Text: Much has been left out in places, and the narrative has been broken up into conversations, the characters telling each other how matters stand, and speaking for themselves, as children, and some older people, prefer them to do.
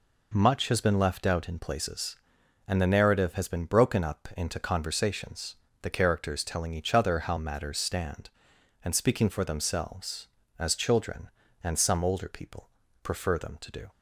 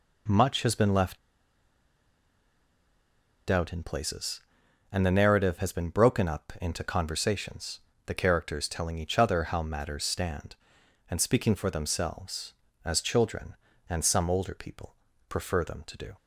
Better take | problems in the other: first | pauses between "left" and "out"; strong; at 1.1 s; 2.3 s long

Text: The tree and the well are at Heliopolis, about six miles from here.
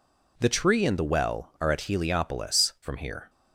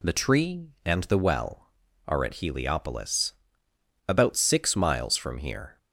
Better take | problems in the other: second | skips "about six miles"; at 2.7 s

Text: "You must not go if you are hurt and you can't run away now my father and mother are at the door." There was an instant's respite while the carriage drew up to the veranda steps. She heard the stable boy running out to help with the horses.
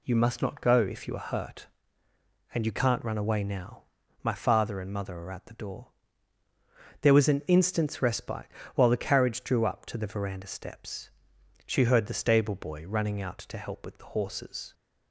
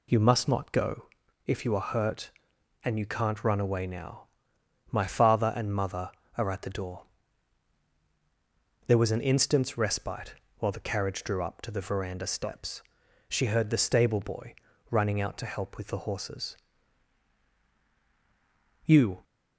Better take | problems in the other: first | pauses between "go" and "if"; at 1.0 s; 0.38 s long // pauses between "now" and "my"; noticeable; at 4.2 s; 0.64 s long; also in the first // pauses between "respite" and "while"; slight; at 10.3 s; 0.24 s long; slight in the first // pauses between "boy" and "running"; slight; at 14.5 s; 0.34 s long // goes on to say "You"; slight; from 18.8 s on; 0.38 s long

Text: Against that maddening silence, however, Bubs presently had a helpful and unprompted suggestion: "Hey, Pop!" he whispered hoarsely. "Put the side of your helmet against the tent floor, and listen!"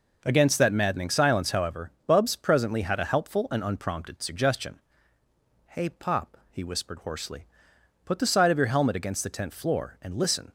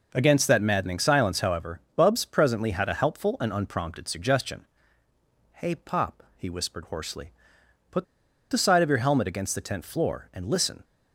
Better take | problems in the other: first | pauses between "Put" and "the"; noticeable; at 8.0 s; 0.46 s long

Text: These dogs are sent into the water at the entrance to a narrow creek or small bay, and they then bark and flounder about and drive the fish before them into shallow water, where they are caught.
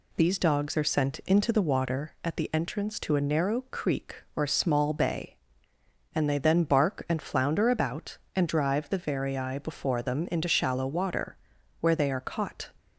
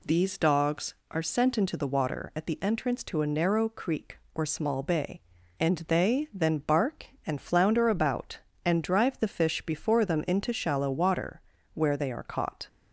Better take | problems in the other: second | says "varii" for "fish"; at 8.9 s

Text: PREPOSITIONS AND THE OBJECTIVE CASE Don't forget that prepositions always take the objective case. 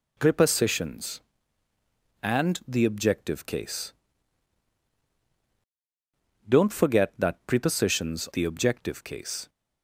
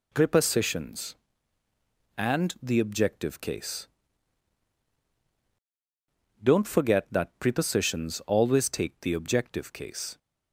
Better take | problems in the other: second | pauses between "CASE" and "Don't"; strong; at 3.9 s; 2.5 s long; strong in the second // skips "always take"; at 8.2 s

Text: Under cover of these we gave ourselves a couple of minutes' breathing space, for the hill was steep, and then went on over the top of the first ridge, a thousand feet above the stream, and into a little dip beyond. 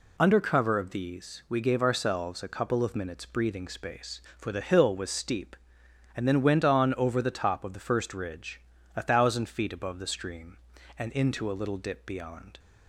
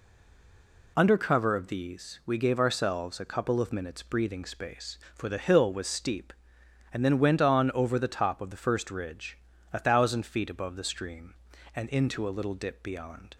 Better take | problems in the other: first | stays silent before the first word; slight; until 0.9 s; 0.9 s long

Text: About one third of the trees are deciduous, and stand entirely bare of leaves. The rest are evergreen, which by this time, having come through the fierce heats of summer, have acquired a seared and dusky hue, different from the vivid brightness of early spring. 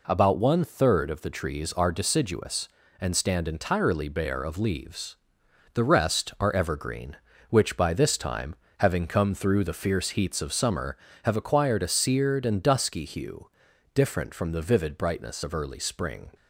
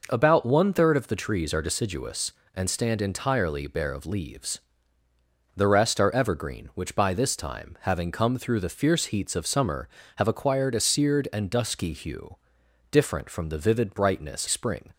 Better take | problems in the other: first | skips "of early"; at 14.4 s

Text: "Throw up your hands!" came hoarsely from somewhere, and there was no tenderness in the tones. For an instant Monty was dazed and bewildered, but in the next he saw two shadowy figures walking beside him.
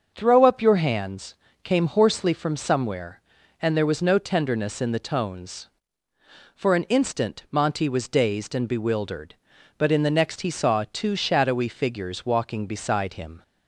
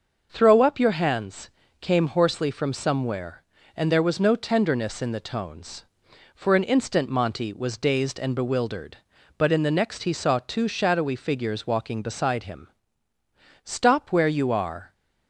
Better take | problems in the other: first | starts louder than the rest; noticeable; until 1.3 s; 6 dB; also in the first // goes on to say "Stop where you are"; noticeable; from 13.6 s on; 1.2 s long

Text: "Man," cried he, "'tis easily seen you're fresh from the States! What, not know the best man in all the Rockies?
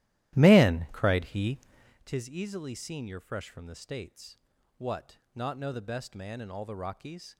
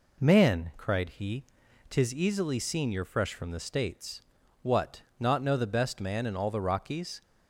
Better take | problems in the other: second | starts louder than the rest; strong; until 2.0 s; 14.5 dB

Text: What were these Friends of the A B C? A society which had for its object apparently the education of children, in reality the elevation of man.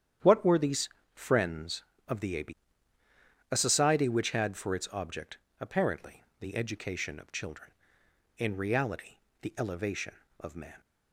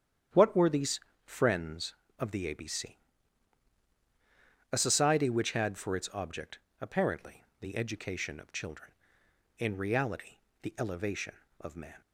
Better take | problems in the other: second | starts louder than the rest; strong; until 1.4 s; 9.5 dB; strong in the second // pauses between "these" and "Friends"; slight; at 0.8 s; 0.26 s long; slight in the second // skips "C"; at 3.0 s // pauses between "object" and "apparently"; slight; at 5.3 s; 0.22 s long; slight in the second // pauses between "apparently" and "the"; slight; at 6.2 s; 0.16 s long; slight in the second // pauses between "reality" and "the"; slight; at 9.1 s; 0.24 s long; slight in the second

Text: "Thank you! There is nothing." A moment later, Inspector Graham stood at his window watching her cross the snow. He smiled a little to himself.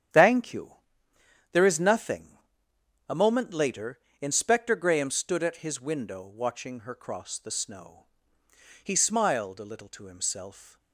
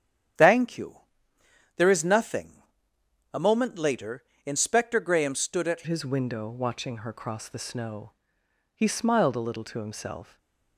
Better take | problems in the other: first | starts louder than the rest; strong; until 2.1 s; 9 dB; strong in the first // changes voice at "his"; from 5.8 s on; 4.5 s long // stays silent after the last word; slight; from 10.2 s on; 0.5 s long

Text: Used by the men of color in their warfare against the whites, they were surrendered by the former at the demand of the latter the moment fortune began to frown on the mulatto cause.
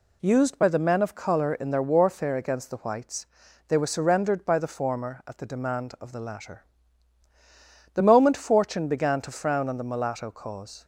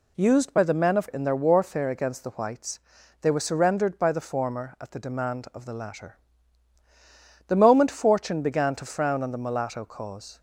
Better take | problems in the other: first | skips "color"; at 1.0 s // pauses between "latter" and "the"; strong; at 6.1 s; 1.3 s long; strong in the first

